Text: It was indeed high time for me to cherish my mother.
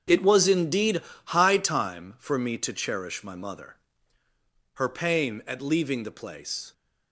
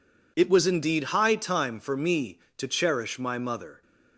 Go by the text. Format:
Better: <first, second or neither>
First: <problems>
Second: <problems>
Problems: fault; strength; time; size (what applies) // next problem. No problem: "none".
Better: second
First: starts louder than the rest; strong; until 1.3 s; 7 dB // pauses between "indeed" and "high"; slight; at 1.0 s; 0.22 s long // goes on to say "Her pain at leaving the place"; strong; from 4.7 s on; 1.9 s long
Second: none